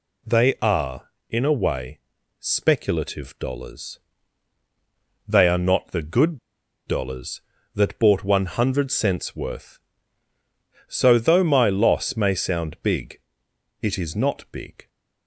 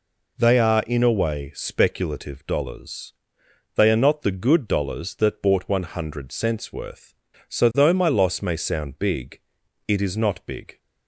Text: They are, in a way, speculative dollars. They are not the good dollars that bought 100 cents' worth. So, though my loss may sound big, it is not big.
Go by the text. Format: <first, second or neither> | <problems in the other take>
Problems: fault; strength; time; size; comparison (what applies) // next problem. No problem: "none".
second | pauses between "good" and "dollars"; noticeable; at 6.3 s; 0.48 s long